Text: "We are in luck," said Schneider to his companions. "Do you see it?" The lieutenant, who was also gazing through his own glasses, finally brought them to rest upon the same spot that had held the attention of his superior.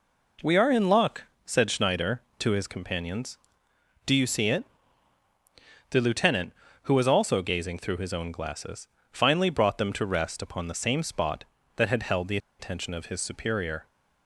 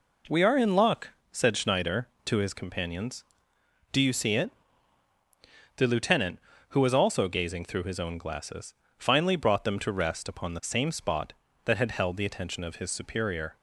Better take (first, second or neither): second